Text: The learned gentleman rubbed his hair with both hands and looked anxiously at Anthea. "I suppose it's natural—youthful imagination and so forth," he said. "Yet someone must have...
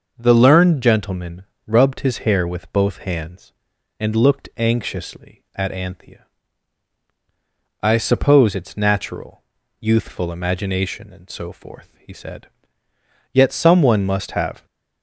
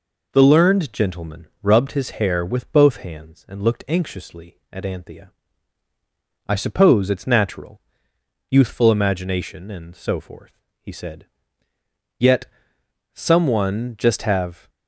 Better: first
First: pauses between "gentleman" and "rubbed"; slight; at 1.4 s; 0.24 s long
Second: pauses between "gentleman" and "rubbed"; slight; at 1.4 s; 0.16 s long // pauses between "Yet" and "someone"; noticeable; at 12.4 s; 0.70 s long // says "just" for "must"; at 13.9 s

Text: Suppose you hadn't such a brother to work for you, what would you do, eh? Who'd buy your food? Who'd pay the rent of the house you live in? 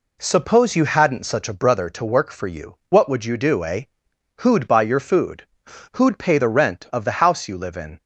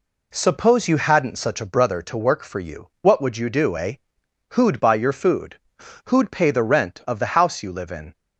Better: neither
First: none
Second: none

